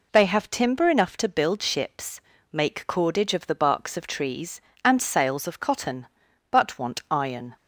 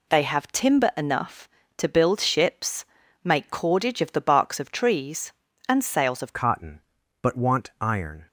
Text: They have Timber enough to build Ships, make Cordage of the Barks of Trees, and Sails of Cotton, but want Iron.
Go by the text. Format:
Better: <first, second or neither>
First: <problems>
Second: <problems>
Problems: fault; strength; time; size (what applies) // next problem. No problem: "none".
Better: first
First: none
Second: changes voice at "Cotton"; from 6.3 s on; 1.9 s long